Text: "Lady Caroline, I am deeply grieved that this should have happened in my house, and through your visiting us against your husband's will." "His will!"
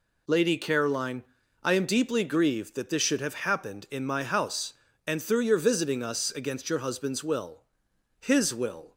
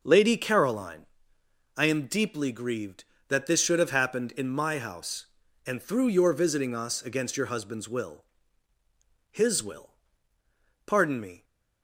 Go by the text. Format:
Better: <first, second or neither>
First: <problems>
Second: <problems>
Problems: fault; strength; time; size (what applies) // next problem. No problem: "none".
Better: first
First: none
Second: goes on to say "Pardon me"; from 10.8 s on; 0.58 s long